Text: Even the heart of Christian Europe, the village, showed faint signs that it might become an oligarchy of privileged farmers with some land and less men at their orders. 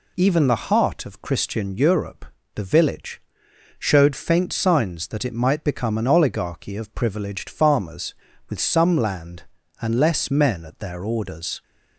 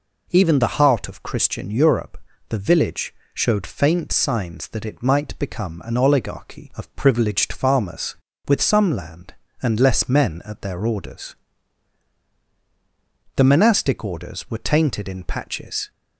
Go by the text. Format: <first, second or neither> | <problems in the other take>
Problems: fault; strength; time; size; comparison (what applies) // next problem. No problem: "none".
first | goes on to say "The Monastic orders were tainted in patches"; strong; from 13.3 s on; 2.5 s long